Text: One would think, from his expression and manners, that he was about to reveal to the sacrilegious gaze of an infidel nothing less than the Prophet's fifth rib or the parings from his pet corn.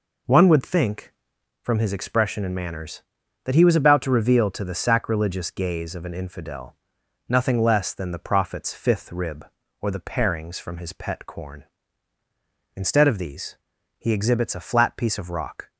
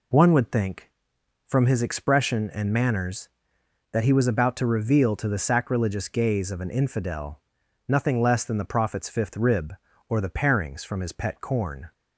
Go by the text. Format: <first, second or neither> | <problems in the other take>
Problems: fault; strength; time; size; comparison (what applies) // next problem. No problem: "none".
second | pauses between "infidel" and "nothing"; noticeable; at 6.7 s; 0.54 s long; noticeable in the second // goes on to say "Instead of these he exhibits a flat piece of rock"; strong; from 12.7 s on; 2.9 s long